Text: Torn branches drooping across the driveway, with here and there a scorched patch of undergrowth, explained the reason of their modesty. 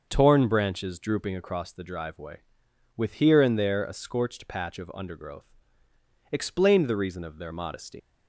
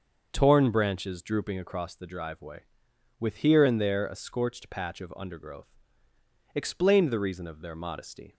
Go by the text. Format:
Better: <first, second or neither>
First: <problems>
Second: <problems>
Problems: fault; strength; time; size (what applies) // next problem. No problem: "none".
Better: second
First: starts louder than the rest; until 1.1 s; 6 dB // leaves "modesty" unfinished; at 7.9 s; 90 ms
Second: starts louder than the rest; until 1.3 s; 6.5 dB